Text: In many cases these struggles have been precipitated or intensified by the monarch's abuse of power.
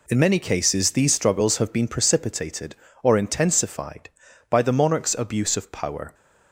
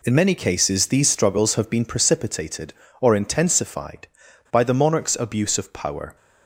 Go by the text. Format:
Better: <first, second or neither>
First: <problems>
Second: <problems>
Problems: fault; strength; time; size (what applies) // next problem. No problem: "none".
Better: neither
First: none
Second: none